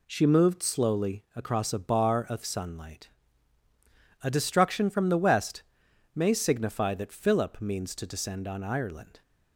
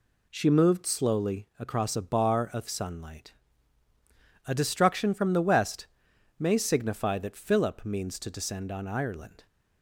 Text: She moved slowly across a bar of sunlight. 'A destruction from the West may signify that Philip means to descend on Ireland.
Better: neither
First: pauses between "West" and "may"; noticeable; at 5.6 s; 0.50 s long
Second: pauses between "West" and "may"; noticeable; at 5.8 s; 0.50 s long

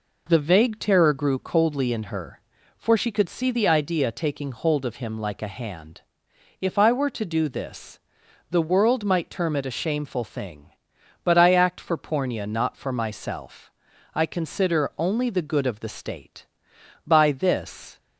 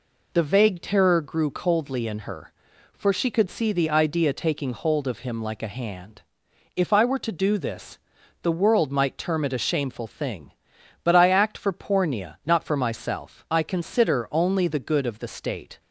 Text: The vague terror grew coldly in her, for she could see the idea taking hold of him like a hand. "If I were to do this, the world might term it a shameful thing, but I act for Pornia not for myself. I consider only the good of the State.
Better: second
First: goes on to say "By this"; noticeable; from 17.0 s on; 0.94 s long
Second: none

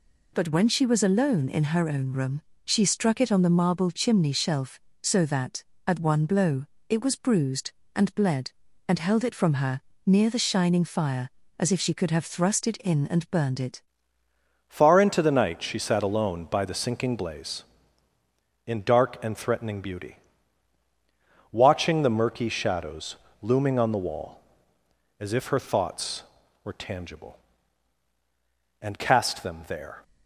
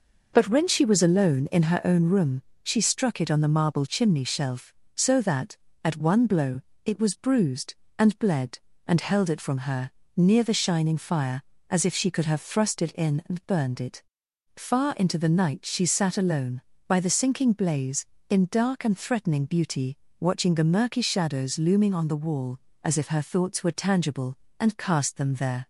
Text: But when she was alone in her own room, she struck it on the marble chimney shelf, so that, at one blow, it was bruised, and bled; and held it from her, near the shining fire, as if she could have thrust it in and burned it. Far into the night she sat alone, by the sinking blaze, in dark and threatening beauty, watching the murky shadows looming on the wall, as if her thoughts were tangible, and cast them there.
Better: second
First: changes voice at "Far"; from 14.6 s on; 15.4 s long // pauses between "shadows" and "looming"; slight; at 23.1 s; 0.24 s long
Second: none

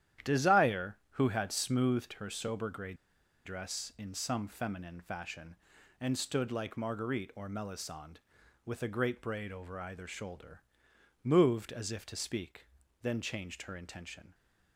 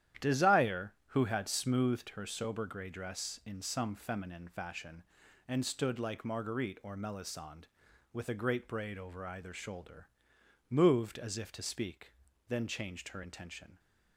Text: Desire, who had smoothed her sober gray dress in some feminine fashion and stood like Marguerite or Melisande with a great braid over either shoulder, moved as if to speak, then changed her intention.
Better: second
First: starts louder than the rest; strong; until 1.4 s; 11 dB // pauses between "gray" and "dress"; noticeable; at 2.9 s; 0.51 s long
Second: starts louder than the rest; strong; until 1.3 s; 11 dB

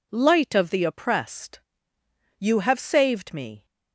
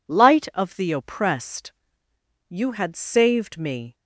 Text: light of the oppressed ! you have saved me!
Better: first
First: none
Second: says "had" for "have"; at 2.7 s

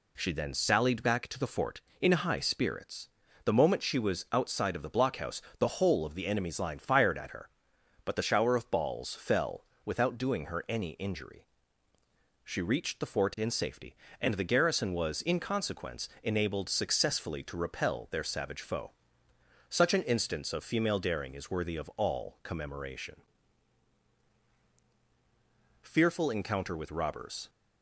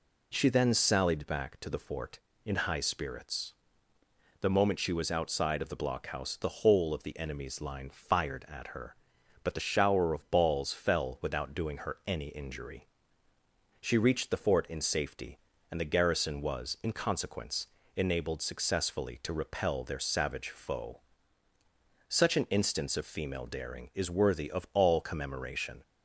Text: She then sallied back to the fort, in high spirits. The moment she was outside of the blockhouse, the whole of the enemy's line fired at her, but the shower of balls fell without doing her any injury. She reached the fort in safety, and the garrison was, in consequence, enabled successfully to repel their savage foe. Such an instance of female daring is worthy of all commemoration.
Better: second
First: pauses between "fell" and "without"; slight; at 9.6 s; 0.20 s long // goes on to say "FEARFUL ENCOUNTER WITH ROBBERS"; strong; from 25.8 s on; 1.6 s long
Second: none

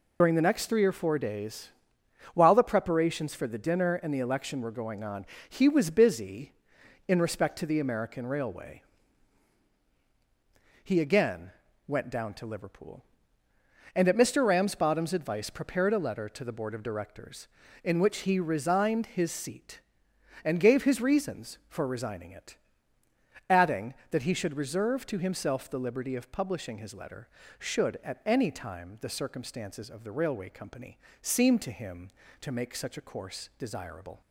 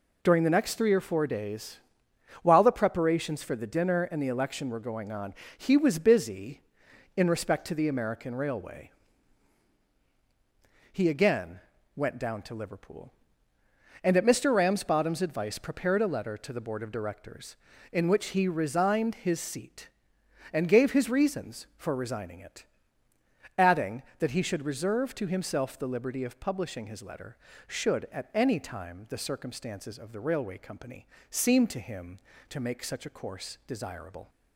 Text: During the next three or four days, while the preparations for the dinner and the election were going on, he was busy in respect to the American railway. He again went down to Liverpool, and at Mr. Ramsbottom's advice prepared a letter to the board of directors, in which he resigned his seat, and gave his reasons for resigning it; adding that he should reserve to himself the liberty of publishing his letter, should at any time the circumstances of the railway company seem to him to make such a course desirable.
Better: second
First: loses the start of "During"; at 0.2 s; 55 ms // pauses between "again" and "went"; slight; at 11.5 s; 0.36 s long // pauses between "company" and "seem"; slight; at 30.9 s; 0.24 s long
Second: pauses between "again" and "went"; slight; at 11.5 s; 0.36 s long // pauses between "company" and "seem"; slight; at 31.0 s; 0.24 s long

